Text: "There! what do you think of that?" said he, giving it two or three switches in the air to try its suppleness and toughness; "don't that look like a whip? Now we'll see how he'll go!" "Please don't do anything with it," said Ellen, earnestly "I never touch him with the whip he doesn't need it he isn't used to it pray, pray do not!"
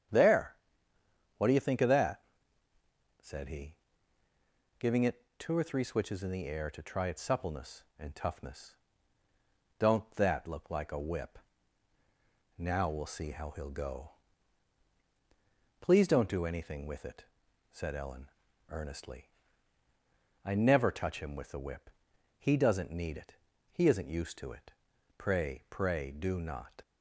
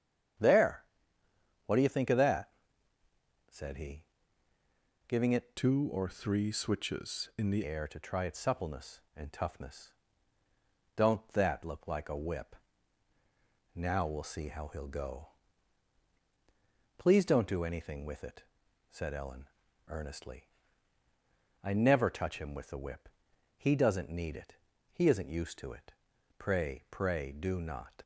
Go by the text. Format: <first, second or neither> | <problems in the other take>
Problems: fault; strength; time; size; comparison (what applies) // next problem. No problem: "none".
first | starts louder than the rest; strong; until 2.2 s; 9 dB; strong in the first // changes voice from "two" to "the"; from 5.5 to 7.6 s; 2.1 s long // pauses between "earnestly" and "I"; at 20.4 s; 1.1 s long; also in the first // pauses between "whip" and "he"; noticeable; at 23.0 s; 0.50 s long; noticeable in the first // pauses between "it" and "he"; slight; at 24.5 s; 0.36 s long; slight in the first // pauses between "it" and "pray"; noticeable; at 25.9 s; 0.48 s long; noticeable in the first